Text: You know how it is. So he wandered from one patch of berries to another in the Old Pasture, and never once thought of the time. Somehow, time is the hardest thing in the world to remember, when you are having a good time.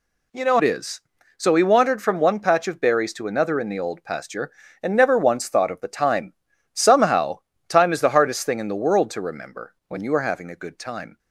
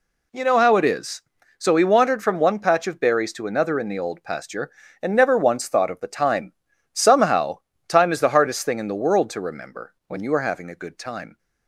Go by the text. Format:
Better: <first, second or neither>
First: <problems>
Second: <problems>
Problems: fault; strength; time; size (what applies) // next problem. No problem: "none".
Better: second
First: skips "how"; at 0.5 s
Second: none